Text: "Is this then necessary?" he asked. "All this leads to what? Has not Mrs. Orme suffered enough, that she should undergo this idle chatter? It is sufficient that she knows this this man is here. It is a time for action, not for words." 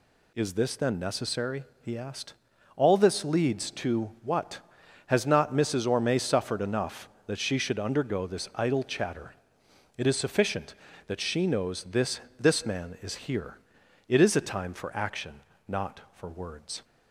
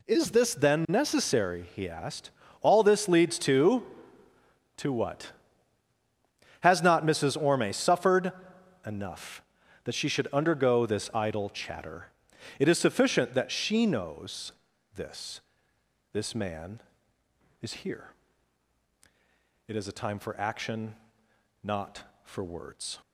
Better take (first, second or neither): first